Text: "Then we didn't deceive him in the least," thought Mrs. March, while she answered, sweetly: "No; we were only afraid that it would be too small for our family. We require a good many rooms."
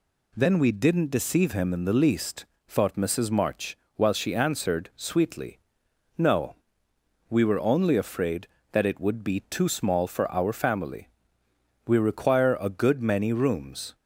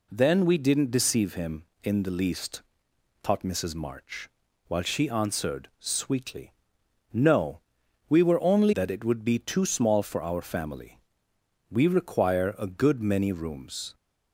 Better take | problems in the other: first | skips "afraid"; at 8.7 s

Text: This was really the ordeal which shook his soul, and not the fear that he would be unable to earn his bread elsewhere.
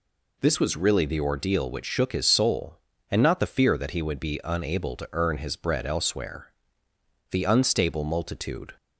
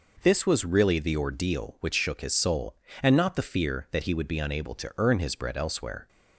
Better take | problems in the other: second | goes on to say "The unstable multitude"; from 7.3 s on; 1.4 s long

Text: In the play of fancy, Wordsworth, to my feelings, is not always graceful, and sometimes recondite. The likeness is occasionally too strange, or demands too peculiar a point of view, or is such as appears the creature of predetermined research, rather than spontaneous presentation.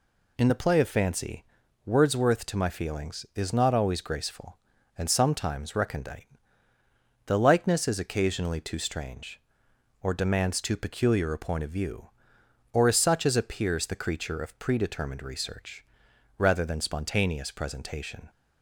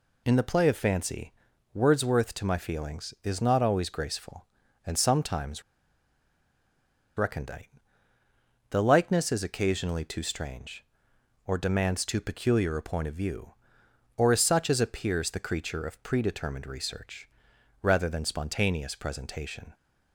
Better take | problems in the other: first | pauses between "sometimes" and "recondite"; strong; at 5.6 s; 1.5 s long

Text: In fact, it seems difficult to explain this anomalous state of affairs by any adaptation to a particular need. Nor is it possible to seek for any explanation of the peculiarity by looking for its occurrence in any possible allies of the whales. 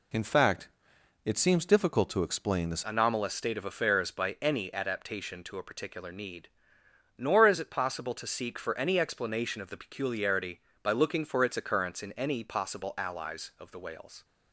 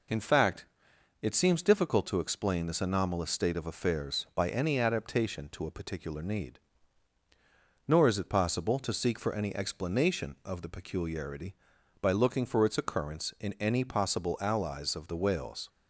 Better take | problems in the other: second | changes voice at "anomalous"; from 2.8 s on; 11.4 s long

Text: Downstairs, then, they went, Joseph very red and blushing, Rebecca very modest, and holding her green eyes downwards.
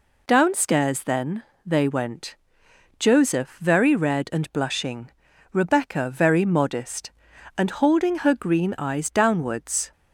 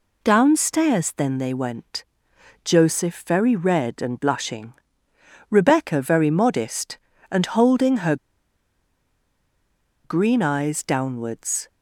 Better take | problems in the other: first | pauses between "her" and "green"; strong; at 8.1 s; 1.8 s long

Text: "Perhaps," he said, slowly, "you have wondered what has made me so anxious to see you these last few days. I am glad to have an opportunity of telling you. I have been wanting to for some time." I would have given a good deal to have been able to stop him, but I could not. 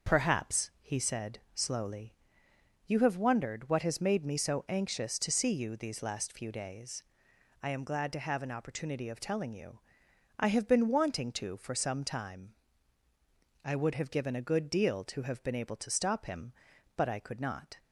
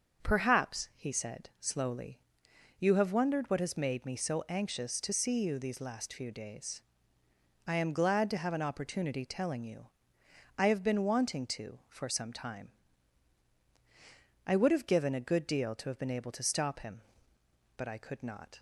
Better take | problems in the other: first | starts louder than the rest; until 1.3 s; 6.5 dB; noticeable in the first // skips "of"; at 9.2 s

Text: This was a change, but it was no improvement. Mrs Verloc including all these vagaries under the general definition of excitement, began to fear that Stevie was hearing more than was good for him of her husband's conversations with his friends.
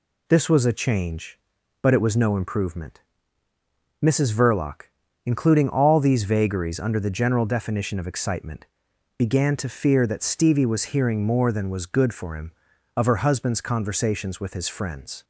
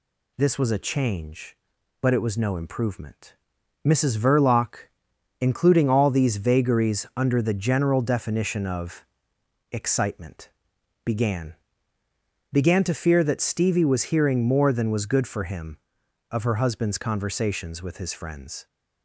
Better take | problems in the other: first | pauses between "Verloc" and "including"; noticeable; at 4.8 s; 0.52 s long; noticeable in the first // pauses between "of" and "excitement"; noticeable; at 9.0 s; 0.70 s long // says "began" twice; at 12.5 s

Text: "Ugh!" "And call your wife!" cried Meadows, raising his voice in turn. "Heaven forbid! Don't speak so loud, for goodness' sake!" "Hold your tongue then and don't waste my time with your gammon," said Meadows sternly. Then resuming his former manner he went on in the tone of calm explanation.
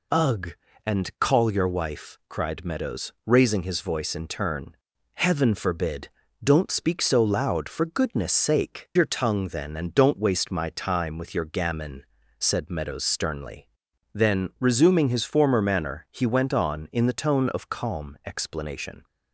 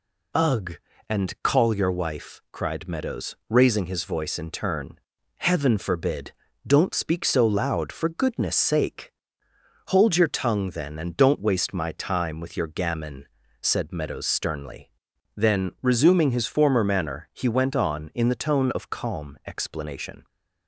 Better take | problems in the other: second | skips "Hold"; at 8.9 s

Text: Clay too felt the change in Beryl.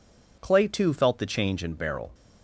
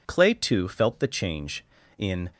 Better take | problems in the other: first | stops before "Beryl"; at 2.3 s

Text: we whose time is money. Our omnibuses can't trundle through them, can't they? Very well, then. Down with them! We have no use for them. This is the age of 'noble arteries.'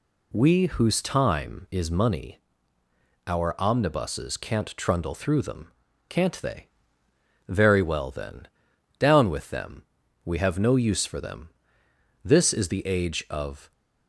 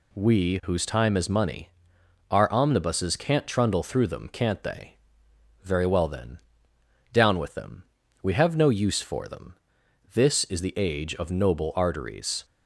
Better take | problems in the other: second | stops before "noble arteries"; at 13.7 s

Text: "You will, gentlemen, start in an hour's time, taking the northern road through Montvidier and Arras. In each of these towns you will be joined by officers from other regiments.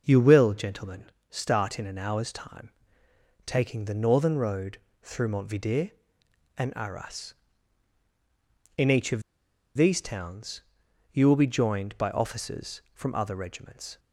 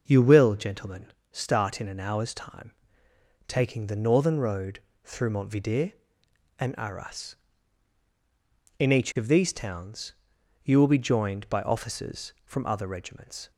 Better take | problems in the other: second | pauses between "road" and "through"; slight; at 4.7 s; 0.24 s long; slight in the second // pauses between "of" and "these"; noticeable; at 9.2 s; 0.54 s long // pauses between "towns" and "you"; noticeable; at 10.6 s; 0.50 s long; noticeable in the second

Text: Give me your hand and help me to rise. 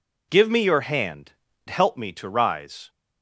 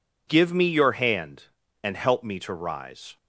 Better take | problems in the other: second | skips "and"; at 1.5 s

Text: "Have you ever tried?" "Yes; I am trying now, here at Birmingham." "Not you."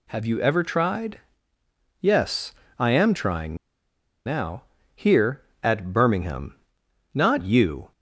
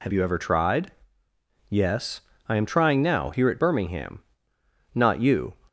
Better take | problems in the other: second | pauses between "trying" and "now"; noticeable; at 3.5 s; 0.68 s long

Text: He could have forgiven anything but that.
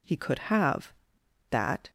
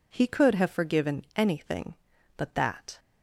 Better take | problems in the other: second | skips "forgiven anything but"; at 1.2 s

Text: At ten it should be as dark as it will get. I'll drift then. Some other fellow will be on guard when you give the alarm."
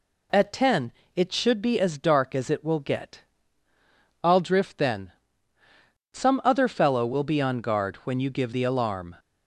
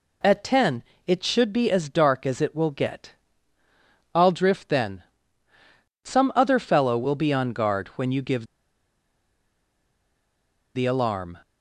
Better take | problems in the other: first | pauses between "ten" and "it"; slight; at 0.8 s; 0.24 s long; slight in the first // pauses between "give" and "the"; strong; at 8.4 s; 2.2 s long

